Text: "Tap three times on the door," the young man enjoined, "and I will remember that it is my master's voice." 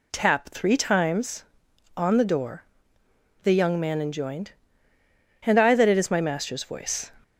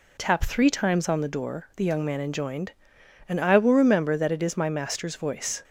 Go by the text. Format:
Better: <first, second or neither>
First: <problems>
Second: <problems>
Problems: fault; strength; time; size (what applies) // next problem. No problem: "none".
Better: second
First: skips "will remember"; at 5.7 s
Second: none